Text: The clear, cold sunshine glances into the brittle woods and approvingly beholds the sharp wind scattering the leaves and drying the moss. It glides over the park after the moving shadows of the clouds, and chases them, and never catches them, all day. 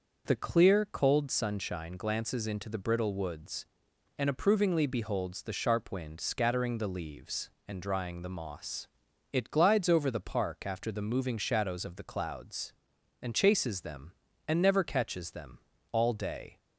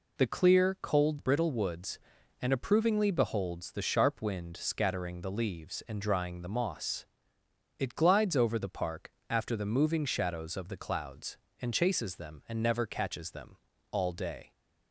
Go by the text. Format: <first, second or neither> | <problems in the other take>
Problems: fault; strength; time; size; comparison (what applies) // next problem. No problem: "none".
first | skips "sunshine glances into the"; at 1.1 s // pauses between "park" and "after"; slight; at 9.1 s; 0.18 s long